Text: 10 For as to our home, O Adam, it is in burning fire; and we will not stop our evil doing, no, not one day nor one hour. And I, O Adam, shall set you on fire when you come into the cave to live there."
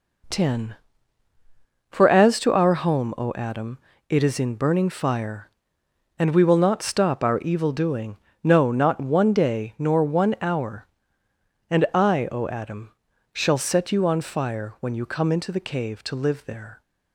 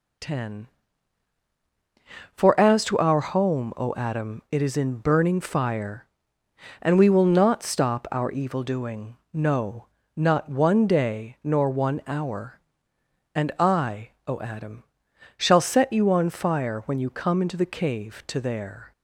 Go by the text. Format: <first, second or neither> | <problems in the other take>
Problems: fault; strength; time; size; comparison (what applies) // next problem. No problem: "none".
first | skips "live"; at 18.3 s